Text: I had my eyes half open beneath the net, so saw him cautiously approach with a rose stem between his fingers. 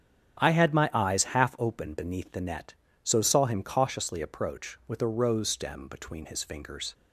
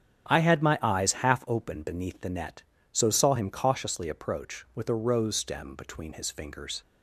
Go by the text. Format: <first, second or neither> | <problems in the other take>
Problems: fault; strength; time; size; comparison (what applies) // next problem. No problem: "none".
neither | starts louder than the rest; strong; the same in both